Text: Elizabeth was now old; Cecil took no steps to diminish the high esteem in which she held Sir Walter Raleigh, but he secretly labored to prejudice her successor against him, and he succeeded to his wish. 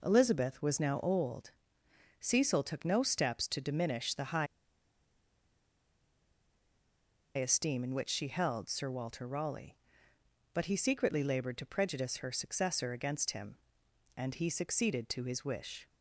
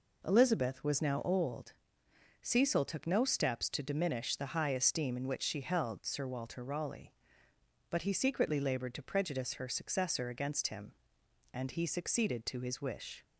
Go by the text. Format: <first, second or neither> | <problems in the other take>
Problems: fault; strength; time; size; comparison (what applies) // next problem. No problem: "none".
second | pauses between "high" and "esteem"; strong; at 4.4 s; 2.9 s long